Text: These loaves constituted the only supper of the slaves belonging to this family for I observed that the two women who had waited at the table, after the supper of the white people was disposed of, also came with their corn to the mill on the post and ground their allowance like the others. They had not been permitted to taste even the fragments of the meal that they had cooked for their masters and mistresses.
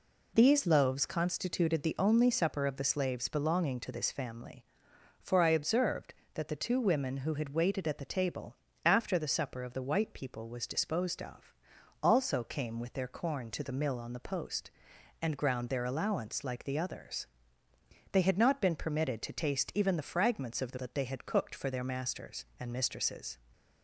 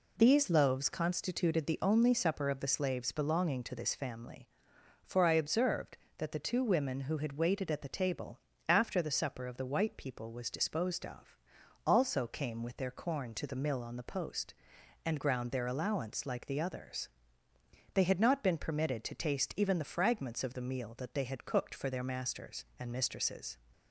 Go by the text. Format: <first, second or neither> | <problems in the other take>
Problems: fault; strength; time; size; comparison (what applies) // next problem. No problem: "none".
second | skips "meal"; at 20.7 s